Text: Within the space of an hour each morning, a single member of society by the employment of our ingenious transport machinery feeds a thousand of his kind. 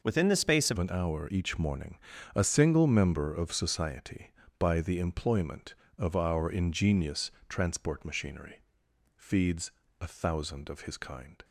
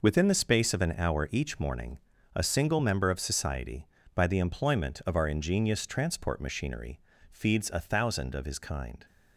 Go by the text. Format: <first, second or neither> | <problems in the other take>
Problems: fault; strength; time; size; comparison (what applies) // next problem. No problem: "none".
second | changes voice at "an"; from 0.7 s on; 10.7 s long // pauses between "ingenious" and "transport"; slight; at 7.2 s; 0.18 s long // pauses between "machinery" and "feeds"; noticeable; at 8.5 s; 0.56 s long; slight in the second // pauses between "feeds" and "a"; slight; at 9.6 s; 0.32 s long